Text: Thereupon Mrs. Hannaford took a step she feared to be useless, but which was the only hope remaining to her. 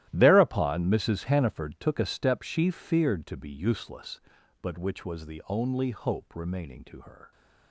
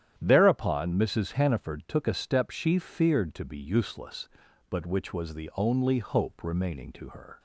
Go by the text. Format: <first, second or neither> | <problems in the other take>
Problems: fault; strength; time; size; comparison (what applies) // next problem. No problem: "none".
second | gets quieter; strong; throughout; 14.5 dB // starts louder than the rest; strong; until 1.1 s; 14 dB; strong in the second